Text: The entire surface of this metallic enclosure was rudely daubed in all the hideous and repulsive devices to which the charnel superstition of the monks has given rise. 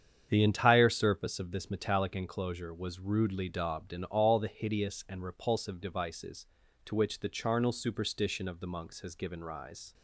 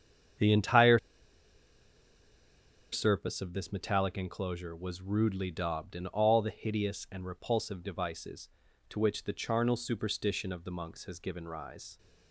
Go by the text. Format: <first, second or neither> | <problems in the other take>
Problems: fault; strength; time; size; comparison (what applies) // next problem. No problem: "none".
first | starts louder than the rest; strong; until 3.3 s; 8 dB; strong in the first // pauses between "entire" and "surface"; strong; at 0.9 s; 1.9 s long